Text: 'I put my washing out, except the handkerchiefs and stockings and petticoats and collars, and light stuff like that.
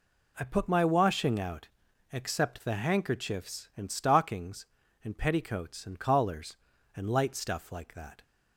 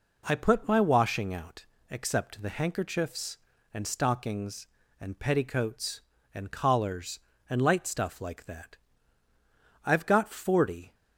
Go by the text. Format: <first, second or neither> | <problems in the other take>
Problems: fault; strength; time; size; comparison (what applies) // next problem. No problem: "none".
first | goes on to say "I've got forty"; noticeable; from 9.8 s on; 1.1 s long